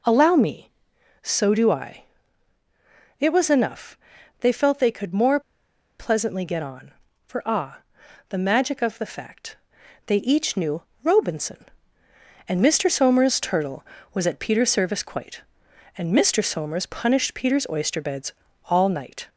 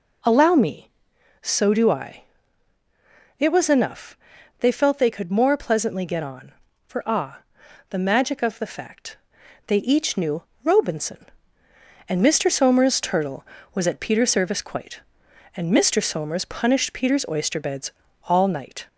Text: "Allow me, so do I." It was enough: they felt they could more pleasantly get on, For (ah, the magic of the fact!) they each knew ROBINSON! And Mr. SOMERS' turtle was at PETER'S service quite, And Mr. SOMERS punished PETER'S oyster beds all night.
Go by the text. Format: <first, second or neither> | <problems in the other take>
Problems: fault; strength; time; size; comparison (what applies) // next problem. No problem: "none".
second | pauses between "more" and "pleasantly"; noticeable; at 5.3 s; 0.59 s long // pauses between "knew" and "ROBINSON"; slight; at 10.8 s; 0.22 s long; slight in the second // pauses between "beds" and "all"; slight; at 18.3 s; 0.32 s long; slight in the second